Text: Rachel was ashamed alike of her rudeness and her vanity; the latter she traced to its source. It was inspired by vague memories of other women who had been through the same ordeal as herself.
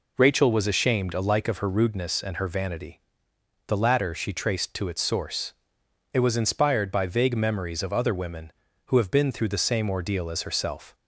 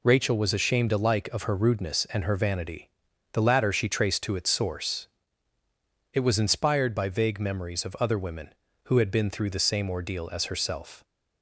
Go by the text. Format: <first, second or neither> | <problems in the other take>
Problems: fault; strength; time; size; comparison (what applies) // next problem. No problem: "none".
second | says "have" for "had"; at 8.9 s